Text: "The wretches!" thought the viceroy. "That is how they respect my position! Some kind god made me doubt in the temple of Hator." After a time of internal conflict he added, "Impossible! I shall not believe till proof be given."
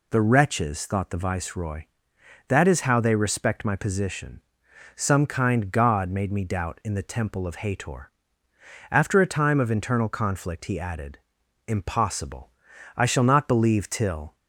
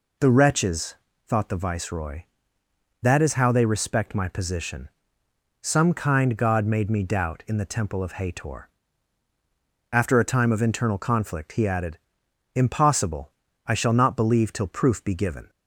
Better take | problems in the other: second | stops before "proof be given"; at 14.3 s

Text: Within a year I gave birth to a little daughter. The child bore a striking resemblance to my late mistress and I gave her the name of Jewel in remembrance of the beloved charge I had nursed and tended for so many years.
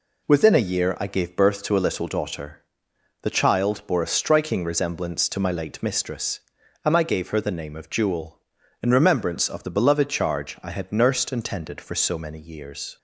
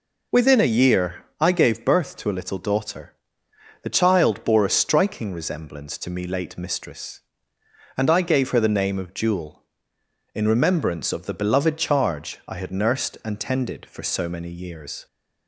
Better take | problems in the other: first | pauses between "year" and "I"; slight; at 1.2 s; 0.16 s long // says "me" for "my"; at 6.1 s

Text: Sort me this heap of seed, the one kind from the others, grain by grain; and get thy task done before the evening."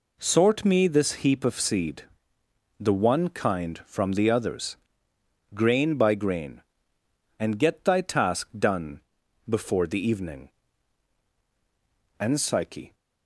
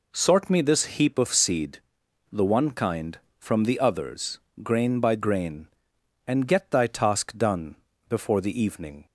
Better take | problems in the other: second | pauses between "done" and "before"; noticeable; at 8.9 s; 0.48 s long; slight in the second // goes on to say "And Psyche"; noticeable; from 12.1 s on; 0.76 s long

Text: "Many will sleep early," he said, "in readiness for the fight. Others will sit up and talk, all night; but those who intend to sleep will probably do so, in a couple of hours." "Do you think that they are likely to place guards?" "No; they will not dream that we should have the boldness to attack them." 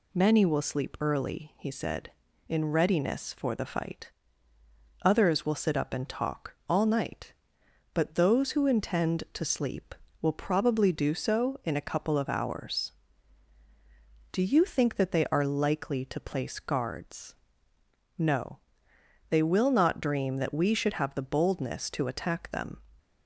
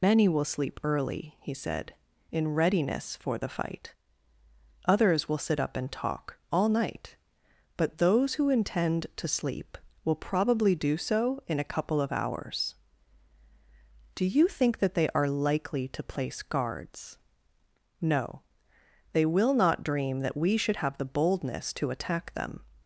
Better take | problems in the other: first | loses the start of "Many"; at 0.0 s; 70 ms

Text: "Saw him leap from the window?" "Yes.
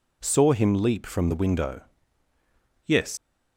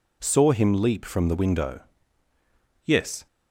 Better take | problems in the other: second | leaves "Yes" unfinished; at 3.1 s; 100 ms

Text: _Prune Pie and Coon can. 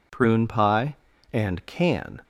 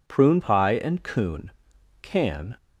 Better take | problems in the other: second | skips "Coon"; at 1.6 s

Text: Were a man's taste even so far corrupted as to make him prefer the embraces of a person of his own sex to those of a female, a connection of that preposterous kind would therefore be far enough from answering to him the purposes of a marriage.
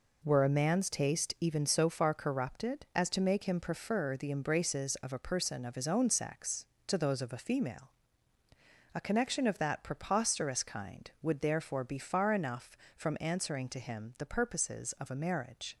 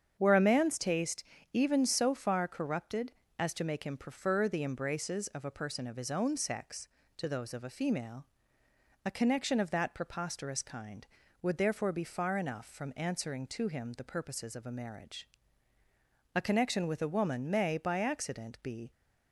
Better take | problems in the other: first | starts louder than the rest; strong; until 1.1 s; 7.5 dB // pauses between "taste" and "even"; slight; at 1.2 s; 0.30 s long // goes on to say "A connection with a woman may by accident be"; strong; from 16.3 s on; 2.5 s long

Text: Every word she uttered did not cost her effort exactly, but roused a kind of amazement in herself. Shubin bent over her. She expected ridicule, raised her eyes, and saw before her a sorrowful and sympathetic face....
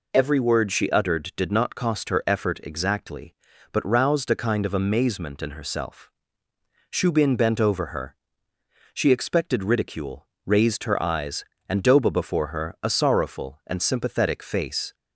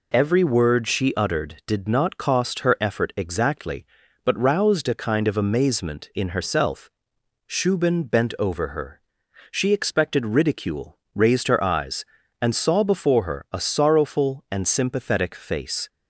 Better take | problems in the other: second | says "doba" for "saw"; at 11.8 s

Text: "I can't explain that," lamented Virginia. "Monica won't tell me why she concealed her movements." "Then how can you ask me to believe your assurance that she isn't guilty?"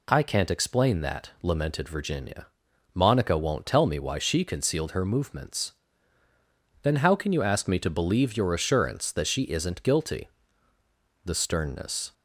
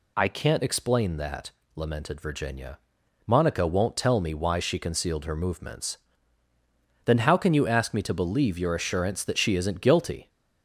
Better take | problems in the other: second | goes on to say "The sternness"; noticeable; from 11.2 s on; 0.88 s long

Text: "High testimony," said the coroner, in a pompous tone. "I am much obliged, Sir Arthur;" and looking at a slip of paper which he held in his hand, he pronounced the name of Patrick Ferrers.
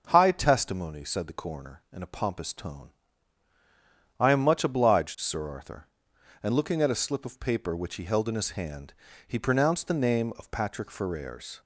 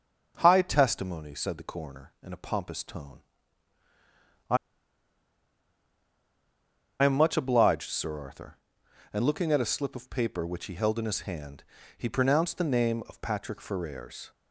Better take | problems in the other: first | starts louder than the rest; until 1.4 s; 6.5 dB; also in the first // pauses between "I" and "am"; strong; at 4.5 s; 2.4 s long

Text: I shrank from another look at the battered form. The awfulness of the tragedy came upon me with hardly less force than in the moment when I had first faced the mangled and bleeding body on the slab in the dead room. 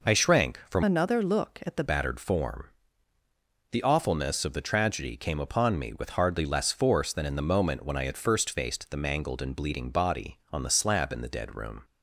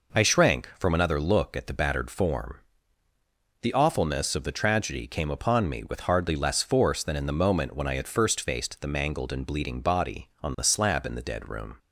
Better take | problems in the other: second | changes voice from "another" to "the"; from 0.8 to 1.8 s; 1.0 s long

